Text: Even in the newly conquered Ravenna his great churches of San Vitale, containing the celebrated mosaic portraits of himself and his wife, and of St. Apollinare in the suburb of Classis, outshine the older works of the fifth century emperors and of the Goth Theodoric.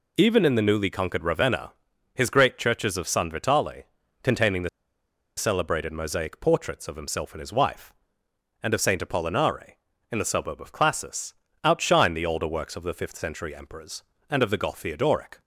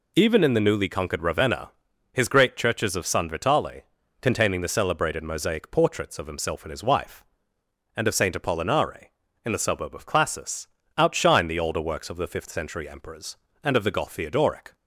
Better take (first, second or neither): second